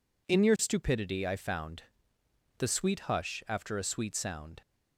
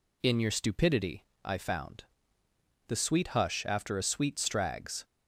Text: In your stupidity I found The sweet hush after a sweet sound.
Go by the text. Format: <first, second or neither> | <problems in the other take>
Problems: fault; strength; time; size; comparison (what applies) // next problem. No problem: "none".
first | pauses between "stupidity" and "I"; slight; at 1.2 s; 0.22 s long // pauses between "found" and "The"; noticeable; at 2.0 s; 0.84 s long; noticeable in the first // says "strags" for "sound"; at 4.3 s